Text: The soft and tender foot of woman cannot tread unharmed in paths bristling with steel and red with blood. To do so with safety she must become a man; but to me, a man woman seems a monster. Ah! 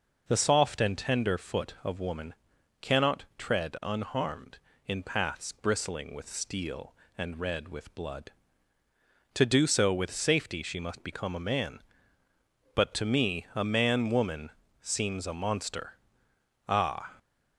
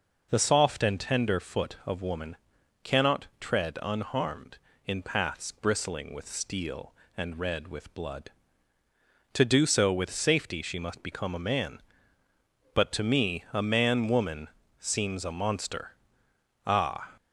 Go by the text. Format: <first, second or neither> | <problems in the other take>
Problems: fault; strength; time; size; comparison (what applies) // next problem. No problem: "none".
neither | pauses between "woman" and "cannot"; noticeable; the same in both // pauses between "woman" and "seems"; slight; the same in both